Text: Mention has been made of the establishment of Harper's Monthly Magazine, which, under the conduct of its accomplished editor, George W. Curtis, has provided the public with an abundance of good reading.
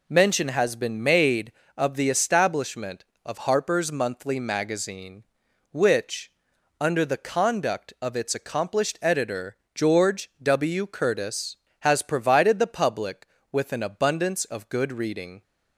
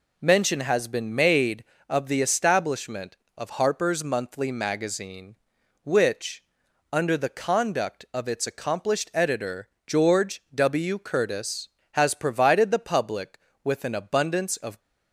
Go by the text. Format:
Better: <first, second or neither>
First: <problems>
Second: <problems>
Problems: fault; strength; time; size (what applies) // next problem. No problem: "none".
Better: first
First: none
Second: stops before "good reading"; at 14.8 s